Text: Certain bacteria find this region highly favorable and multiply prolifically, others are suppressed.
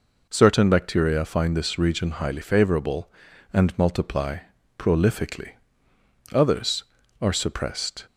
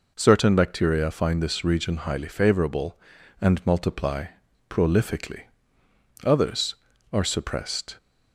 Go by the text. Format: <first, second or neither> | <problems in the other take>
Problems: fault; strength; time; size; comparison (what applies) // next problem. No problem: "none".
neither | pauses between "multiply" and "prolifically"; the same in both